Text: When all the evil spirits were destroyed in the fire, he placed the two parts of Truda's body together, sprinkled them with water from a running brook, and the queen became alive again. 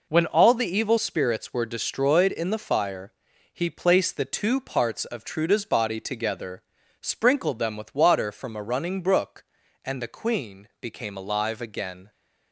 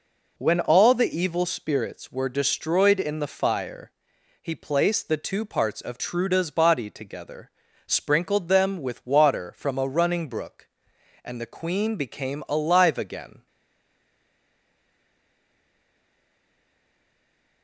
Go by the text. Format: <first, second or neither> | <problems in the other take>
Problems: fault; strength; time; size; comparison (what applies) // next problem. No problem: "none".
first | stays silent after the last word; strong; from 13.4 s on; 4.2 s long